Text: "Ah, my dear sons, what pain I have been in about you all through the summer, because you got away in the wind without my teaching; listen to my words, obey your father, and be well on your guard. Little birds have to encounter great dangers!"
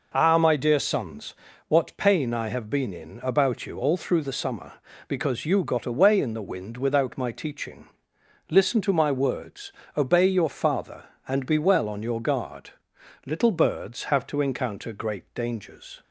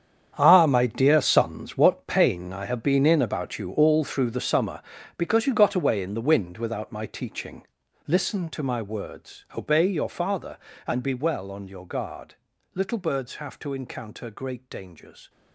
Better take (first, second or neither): first